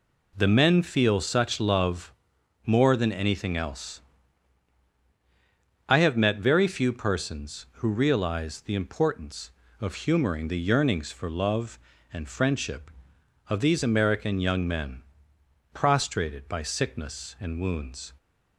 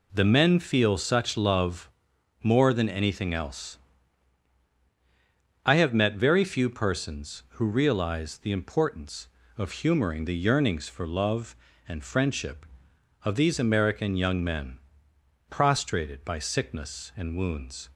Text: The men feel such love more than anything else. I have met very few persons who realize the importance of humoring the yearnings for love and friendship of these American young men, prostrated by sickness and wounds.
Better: neither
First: pauses between "love" and "more"; noticeable; at 2.1 s; 0.54 s long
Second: pauses between "love" and "more"; noticeable; at 1.8 s; 0.54 s long

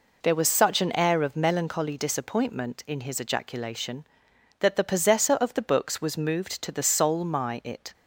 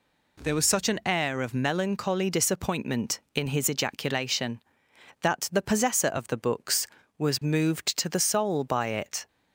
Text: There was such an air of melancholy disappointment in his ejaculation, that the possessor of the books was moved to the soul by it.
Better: second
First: says "my" for "by"; at 7.2 s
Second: none

